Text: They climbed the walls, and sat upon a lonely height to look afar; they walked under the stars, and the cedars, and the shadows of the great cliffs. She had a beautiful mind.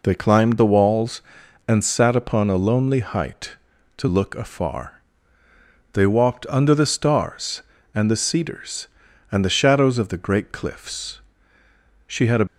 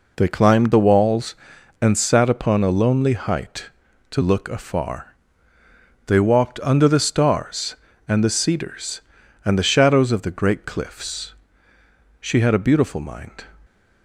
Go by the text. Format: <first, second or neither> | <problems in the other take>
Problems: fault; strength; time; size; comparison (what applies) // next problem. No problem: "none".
second | stops before "beautiful mind"; at 12.4 s